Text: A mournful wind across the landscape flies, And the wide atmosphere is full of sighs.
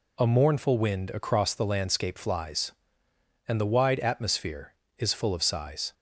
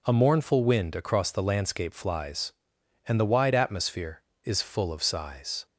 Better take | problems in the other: neither | none

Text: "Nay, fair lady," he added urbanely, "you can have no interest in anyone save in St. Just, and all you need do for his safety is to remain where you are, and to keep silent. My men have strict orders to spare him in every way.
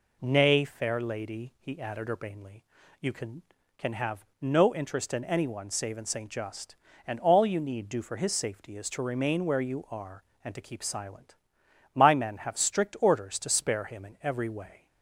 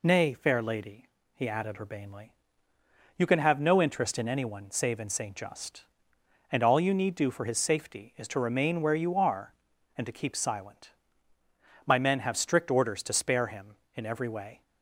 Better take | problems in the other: second | says "can" twice; at 3.7 s // pauses between "have" and "no"; slight; at 4.2 s; 0.16 s long

